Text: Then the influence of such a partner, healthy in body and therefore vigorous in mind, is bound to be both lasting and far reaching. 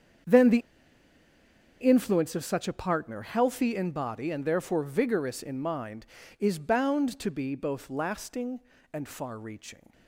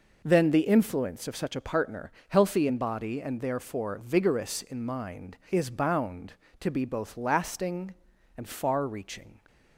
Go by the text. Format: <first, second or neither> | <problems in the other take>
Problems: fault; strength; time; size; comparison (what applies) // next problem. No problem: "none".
second | starts louder than the rest; strong; until 2.4 s; 7.5 dB // pauses between "the" and "influence"; at 0.5 s; 1.2 s long